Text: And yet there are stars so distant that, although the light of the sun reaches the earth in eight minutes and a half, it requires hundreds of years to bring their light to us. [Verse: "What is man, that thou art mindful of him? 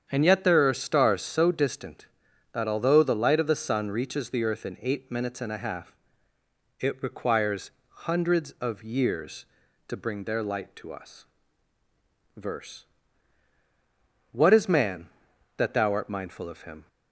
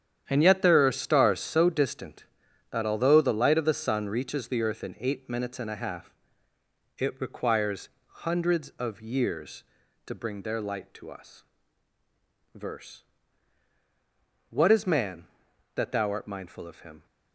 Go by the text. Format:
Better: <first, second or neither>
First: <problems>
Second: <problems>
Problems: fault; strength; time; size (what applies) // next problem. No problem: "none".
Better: first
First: starts louder than the rest; strong; until 1.1 s; 8 dB // pauses between "requires" and "hundreds"; slight; at 7.7 s; 0.18 s long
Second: gets quieter; strong; throughout; 11.5 dB // starts louder than the rest; strong; until 1.3 s; 9.5 dB // pauses between "requires" and "hundreds"; slight; at 7.8 s; 0.18 s long